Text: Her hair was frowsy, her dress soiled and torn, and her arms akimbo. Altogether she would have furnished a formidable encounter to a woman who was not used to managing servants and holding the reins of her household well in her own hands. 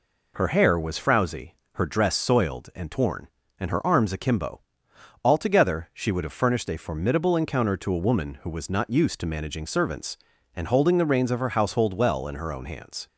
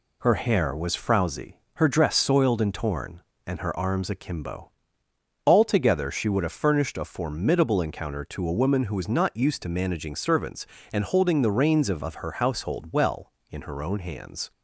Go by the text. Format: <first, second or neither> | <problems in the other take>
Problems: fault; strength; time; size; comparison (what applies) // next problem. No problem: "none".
first | says "of" twice; at 12.0 s